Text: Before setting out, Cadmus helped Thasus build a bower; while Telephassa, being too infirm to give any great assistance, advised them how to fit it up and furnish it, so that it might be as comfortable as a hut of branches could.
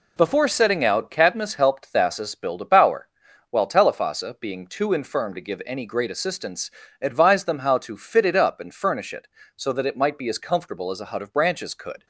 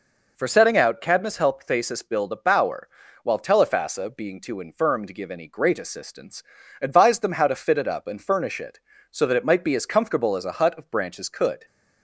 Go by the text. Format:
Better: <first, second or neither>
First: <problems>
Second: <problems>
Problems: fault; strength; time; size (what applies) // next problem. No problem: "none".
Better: first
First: none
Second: says "For" for "Before"; at 0.3 s